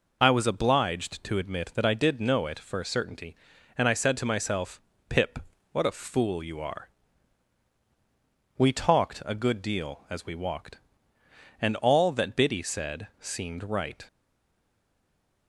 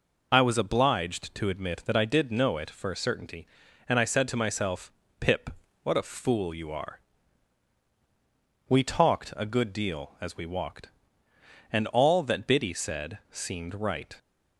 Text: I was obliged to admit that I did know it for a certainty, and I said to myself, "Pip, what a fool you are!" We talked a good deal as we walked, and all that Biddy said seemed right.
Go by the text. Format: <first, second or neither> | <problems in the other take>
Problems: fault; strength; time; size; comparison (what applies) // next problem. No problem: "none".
second | stays silent after the last word; noticeable; from 14.0 s on; 1.4 s long